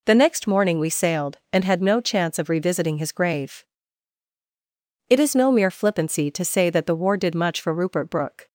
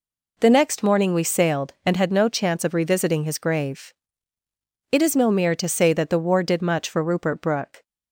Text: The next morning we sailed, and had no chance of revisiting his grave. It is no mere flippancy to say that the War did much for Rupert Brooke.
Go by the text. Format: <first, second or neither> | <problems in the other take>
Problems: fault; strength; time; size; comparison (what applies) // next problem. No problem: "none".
first | skips "flippancy"; at 5.5 s